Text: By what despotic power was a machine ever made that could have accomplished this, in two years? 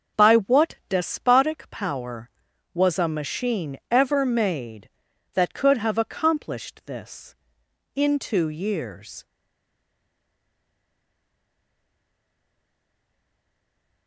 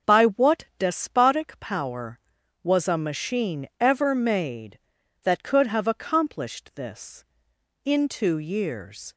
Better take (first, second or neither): second